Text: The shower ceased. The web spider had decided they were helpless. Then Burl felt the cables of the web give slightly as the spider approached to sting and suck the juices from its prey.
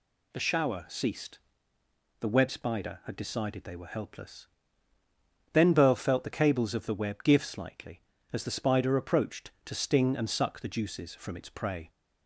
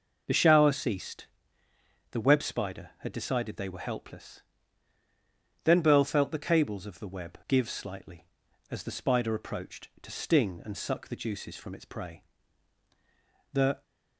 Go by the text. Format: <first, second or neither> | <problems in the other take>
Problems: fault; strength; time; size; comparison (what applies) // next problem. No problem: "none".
first | goes on to say "The"; slight; from 13.5 s on; 0.30 s long